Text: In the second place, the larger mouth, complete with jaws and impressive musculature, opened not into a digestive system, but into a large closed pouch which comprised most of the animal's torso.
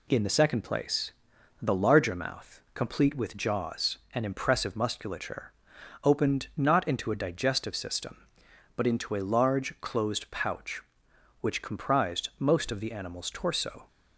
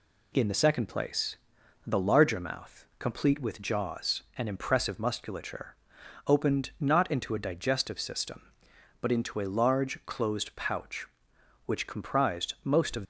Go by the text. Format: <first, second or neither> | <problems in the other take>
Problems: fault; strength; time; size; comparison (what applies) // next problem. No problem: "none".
first | stops before "the animal's torso"; at 13.0 s